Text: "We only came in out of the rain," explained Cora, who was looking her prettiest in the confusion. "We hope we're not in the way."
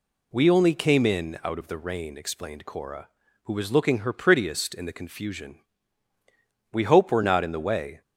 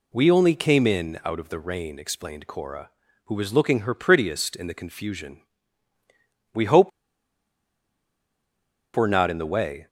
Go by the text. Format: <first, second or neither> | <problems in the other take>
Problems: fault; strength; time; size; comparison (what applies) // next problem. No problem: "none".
first | pauses between "hope" and "we're"; strong; at 6.9 s; 2.0 s long